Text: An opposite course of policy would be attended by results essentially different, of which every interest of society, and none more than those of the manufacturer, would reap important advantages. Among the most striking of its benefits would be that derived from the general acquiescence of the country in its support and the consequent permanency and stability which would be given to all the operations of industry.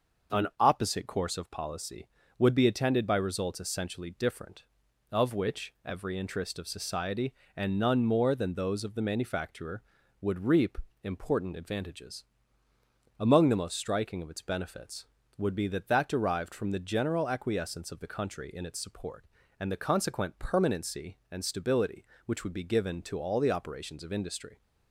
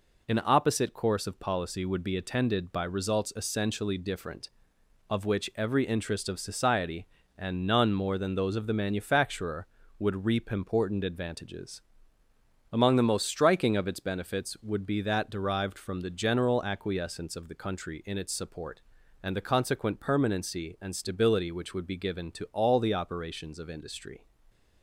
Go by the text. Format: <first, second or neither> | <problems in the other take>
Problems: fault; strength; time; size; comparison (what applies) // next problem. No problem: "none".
second | starts louder than the rest; noticeable; until 1.4 s; 6 dB // pauses between "reap" and "important"; slight; at 10.7 s; 0.26 s long // says "that" twice; at 15.8 s